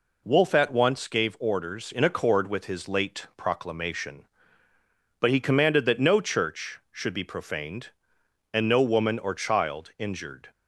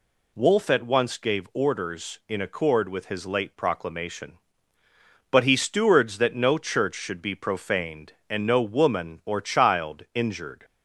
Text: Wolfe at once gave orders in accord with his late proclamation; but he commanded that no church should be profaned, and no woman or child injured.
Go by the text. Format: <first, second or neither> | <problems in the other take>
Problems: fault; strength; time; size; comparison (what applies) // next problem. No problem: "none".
first | says "stewards" for "commanded"; at 5.5 s